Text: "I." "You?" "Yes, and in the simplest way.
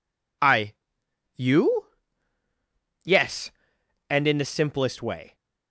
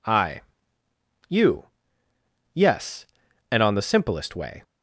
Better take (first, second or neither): first